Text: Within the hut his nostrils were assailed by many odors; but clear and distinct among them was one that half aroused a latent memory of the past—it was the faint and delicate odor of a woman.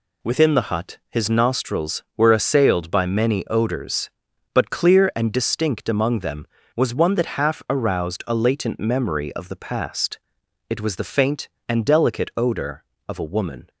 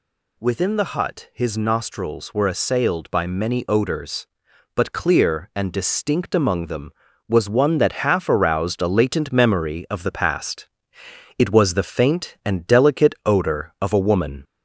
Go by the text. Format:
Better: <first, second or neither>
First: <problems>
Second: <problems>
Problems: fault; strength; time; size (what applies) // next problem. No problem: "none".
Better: first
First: none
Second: gets louder; slight; throughout; 2.5 dB